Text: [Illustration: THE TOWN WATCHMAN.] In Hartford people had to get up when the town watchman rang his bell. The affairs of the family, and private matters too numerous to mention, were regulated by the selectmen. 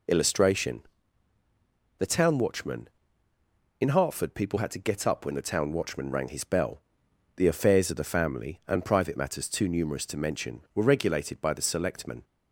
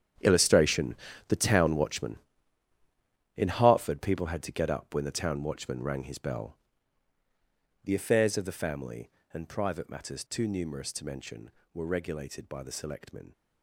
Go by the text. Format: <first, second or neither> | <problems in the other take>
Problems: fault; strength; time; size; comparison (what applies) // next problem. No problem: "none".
first | gets quieter; strong; throughout; 14 dB